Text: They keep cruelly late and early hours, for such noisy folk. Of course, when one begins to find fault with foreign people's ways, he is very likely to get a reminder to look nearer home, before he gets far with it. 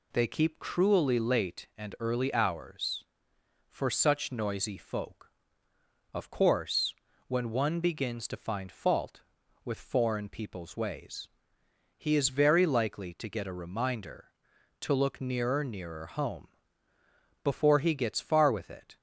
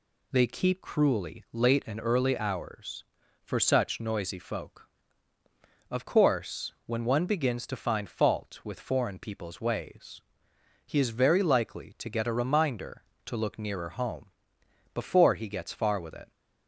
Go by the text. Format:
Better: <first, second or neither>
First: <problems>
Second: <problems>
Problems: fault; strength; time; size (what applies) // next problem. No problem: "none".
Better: second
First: says "nearer" twice; at 15.6 s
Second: none